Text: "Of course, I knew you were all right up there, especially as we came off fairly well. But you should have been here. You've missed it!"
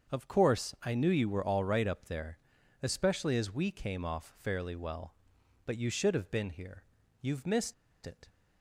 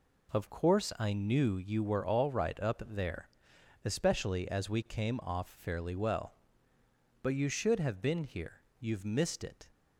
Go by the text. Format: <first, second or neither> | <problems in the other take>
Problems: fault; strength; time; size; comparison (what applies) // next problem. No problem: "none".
second | starts louder than the rest; until 1.1 s; 6.5 dB // pauses between "missed" and "it"; slight; at 7.7 s; 0.31 s long